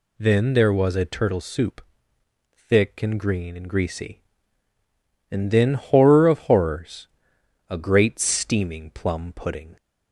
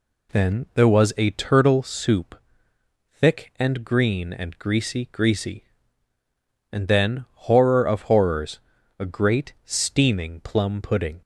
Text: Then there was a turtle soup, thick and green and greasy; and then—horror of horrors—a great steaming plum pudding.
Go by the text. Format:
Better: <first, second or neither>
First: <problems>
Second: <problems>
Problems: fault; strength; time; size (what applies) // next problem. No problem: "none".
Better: first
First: none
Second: says "greasy" twice; at 5.1 s